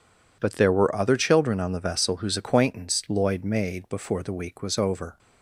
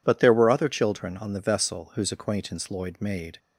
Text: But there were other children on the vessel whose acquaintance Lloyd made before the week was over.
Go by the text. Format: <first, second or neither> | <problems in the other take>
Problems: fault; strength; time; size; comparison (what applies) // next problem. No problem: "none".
first | stops before "before the week was over"; at 3.3 s